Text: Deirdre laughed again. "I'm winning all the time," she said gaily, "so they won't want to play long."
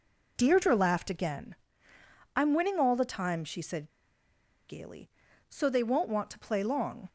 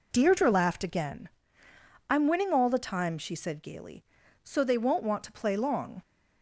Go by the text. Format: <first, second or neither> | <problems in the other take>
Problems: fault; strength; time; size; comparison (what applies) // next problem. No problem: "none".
second | pauses between "said" and "gaily"; noticeable; at 3.8 s; 0.79 s long